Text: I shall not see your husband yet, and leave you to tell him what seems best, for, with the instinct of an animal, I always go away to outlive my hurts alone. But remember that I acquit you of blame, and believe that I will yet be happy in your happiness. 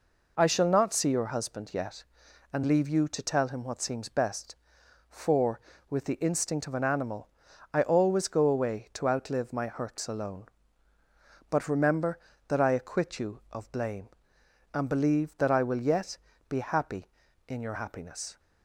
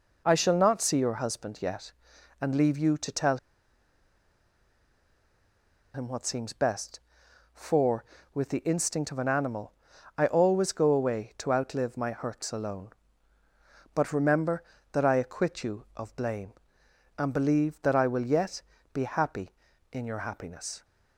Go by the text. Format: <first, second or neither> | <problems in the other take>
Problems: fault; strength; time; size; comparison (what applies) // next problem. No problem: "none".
first | pauses between "tell" and "him"; strong; at 3.3 s; 2.5 s long // pauses between "yet" and "be"; slight; at 18.6 s; 0.30 s long; slight in the first